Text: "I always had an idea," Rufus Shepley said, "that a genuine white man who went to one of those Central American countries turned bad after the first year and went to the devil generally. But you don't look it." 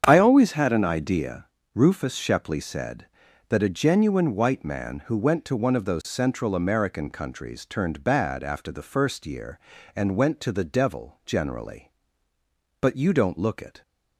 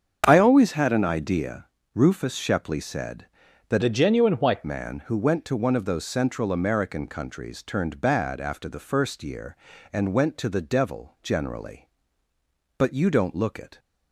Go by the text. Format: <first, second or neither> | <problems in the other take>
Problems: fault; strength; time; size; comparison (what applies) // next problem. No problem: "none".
first | starts louder than the rest; strong; until 1.2 s; 7 dB; strong in the first // changes voice from "a" to "white"; from 3.8 to 4.6 s; 0.8 s long